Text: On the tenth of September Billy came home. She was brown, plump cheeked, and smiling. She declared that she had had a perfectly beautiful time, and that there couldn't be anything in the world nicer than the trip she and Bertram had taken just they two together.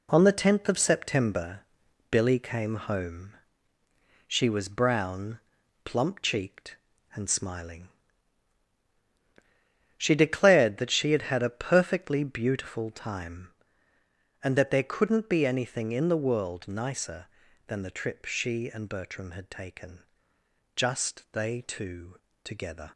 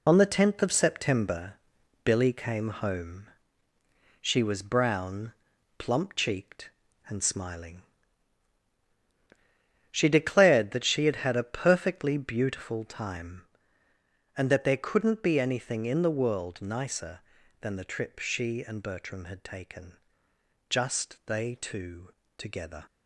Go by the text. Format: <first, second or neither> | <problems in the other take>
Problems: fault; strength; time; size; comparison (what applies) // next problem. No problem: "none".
first | loses the start of "On"; at 0.0 s; 45 ms // pauses between "September" and "Billy"; noticeable; at 1.5 s; 0.50 s long; noticeable in the first // pauses between "taken" and "just"; noticeable; at 19.9 s; 0.72 s long; noticeable in the first // pauses between "two" and "together"; slight; at 22.1 s; 0.24 s long; slight in the first